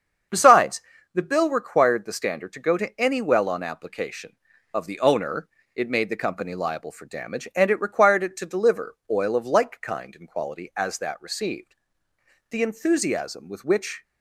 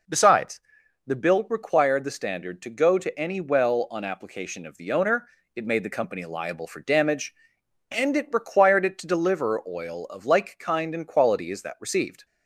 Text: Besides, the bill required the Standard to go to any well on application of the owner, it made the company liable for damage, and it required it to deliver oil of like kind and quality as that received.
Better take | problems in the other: second | starts louder than the rest; strong; until 1.6 s; 7 dB // pauses between "deliver" and "oil"; slight; at 8.9 s; 0.16 s long // goes on to say "The enthusiasm with which"; from 12.4 s on; 1.5 s long

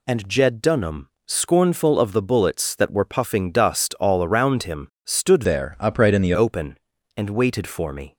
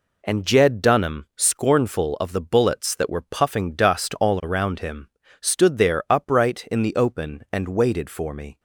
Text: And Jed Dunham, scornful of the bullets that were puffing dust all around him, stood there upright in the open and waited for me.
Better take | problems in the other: second | changes voice from "there" to "the"; from 5.4 to 6.3 s; 0.9 s long

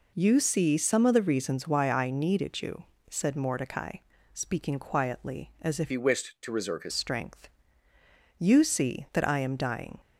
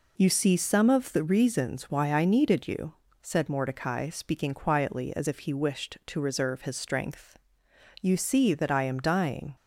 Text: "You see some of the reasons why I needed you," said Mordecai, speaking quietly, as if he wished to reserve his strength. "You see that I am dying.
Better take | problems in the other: second | changes voice from "he" to "his"; from 5.8 to 6.9 s; 1.1 s long

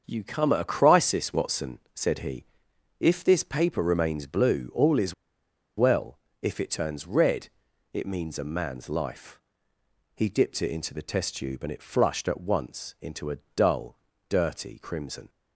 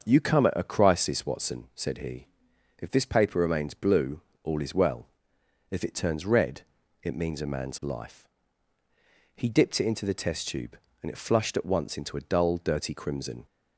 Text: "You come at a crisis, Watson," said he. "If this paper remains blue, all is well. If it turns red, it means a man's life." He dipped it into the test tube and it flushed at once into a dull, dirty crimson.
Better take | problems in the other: second | starts louder than the rest; until 1.0 s; 6.5 dB; also in the second // pauses between "is" and "well"; noticeable; at 5.1 s; 0.63 s long // pauses between "a" and "dull"; slight; at 13.3 s; 0.18 s long

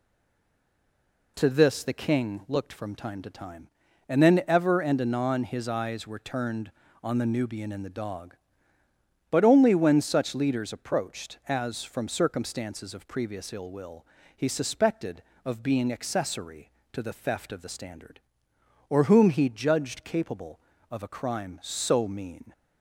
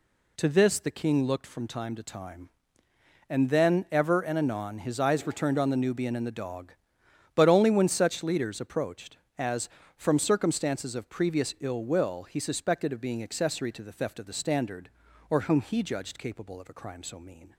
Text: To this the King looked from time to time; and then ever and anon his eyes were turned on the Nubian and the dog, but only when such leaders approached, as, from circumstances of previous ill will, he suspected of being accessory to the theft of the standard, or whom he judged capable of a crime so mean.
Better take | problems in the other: second | stays silent before the first word; noticeable; until 1.3 s; 1.3 s long

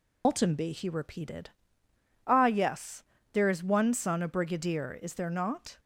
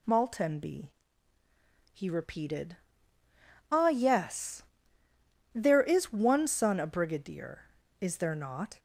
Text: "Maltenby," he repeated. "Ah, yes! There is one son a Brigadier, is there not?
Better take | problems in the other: second | loses the start of "Maltenby"; at 0.2 s; 160 ms

